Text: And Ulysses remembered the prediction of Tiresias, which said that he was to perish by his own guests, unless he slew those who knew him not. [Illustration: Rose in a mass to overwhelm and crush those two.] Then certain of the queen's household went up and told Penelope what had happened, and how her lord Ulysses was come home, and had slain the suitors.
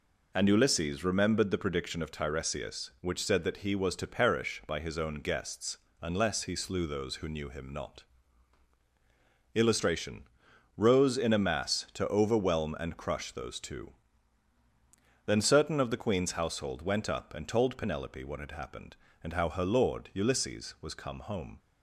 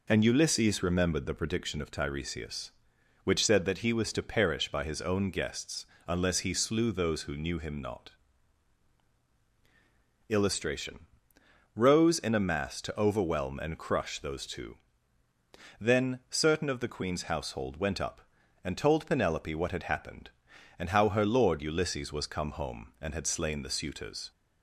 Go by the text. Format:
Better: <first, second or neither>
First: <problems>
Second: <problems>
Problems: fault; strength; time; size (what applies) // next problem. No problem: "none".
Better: second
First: stops before "and had slain the suitors"; at 21.5 s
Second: none